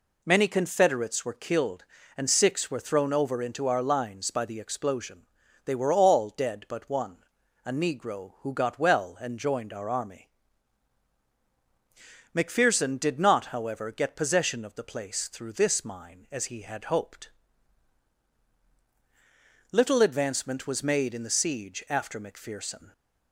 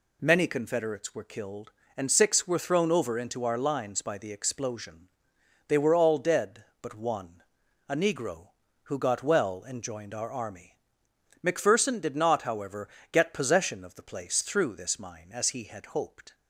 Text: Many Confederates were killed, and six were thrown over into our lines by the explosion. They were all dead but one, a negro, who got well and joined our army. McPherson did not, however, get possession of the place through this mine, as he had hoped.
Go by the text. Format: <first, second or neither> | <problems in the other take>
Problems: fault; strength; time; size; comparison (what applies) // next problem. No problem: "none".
second | goes on to say "Little advancement was made in the siege after McPherson"; strong; from 19.7 s on; 3.2 s long